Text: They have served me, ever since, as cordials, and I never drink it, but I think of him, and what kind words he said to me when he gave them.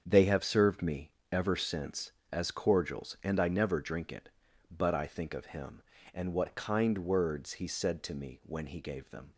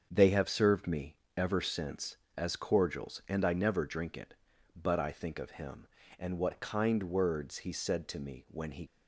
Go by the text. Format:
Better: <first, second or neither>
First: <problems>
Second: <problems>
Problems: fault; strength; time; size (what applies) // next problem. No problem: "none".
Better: first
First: starts louder than the rest; strong; until 1.0 s; 7.5 dB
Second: starts louder than the rest; until 1.1 s; 7 dB // stops before "gave them"; at 8.8 s